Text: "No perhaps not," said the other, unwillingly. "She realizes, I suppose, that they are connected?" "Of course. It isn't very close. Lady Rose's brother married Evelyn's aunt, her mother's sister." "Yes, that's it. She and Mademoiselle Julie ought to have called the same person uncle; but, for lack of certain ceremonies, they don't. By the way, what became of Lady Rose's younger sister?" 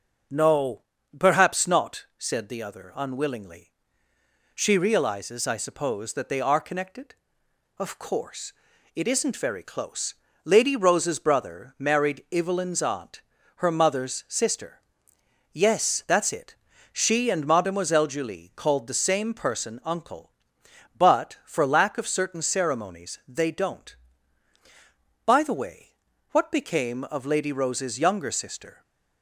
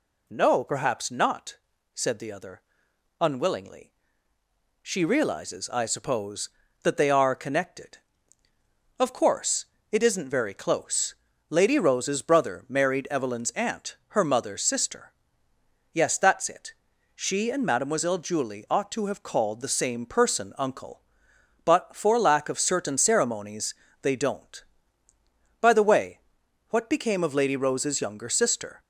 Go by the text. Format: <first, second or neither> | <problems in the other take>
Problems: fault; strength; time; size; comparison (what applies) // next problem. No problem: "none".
second | pauses between "No" and "perhaps"; slight; at 0.8 s; 0.36 s long // skips "ought to have"; at 18.5 s